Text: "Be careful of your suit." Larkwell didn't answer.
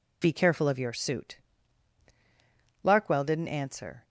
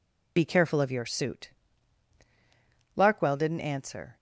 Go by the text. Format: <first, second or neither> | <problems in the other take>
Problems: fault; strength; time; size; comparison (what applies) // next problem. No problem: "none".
first | loses the start of "Be"; at 0.3 s; 20 ms